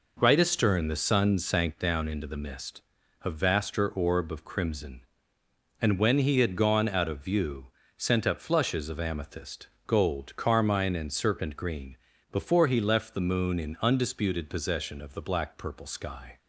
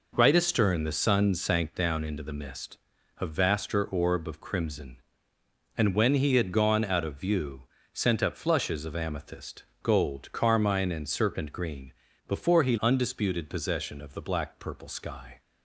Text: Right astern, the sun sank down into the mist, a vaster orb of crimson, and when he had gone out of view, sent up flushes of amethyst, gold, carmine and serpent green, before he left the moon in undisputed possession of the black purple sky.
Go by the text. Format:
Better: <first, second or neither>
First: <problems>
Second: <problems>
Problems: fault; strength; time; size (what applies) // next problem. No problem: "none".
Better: first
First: none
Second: skips "left the moon in"; at 12.7 s